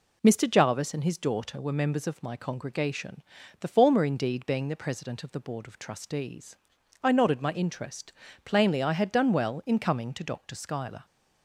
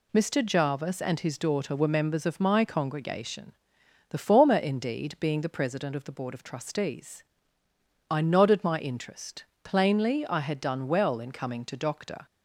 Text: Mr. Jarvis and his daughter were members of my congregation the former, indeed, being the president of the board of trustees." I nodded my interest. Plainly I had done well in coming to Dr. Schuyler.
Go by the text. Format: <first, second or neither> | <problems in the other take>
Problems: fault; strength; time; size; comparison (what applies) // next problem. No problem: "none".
first | pauses between "congregation" and "the"; noticeable; at 3.5 s; 0.56 s long; also in the first // stops before "Schuyler"; at 12.2 s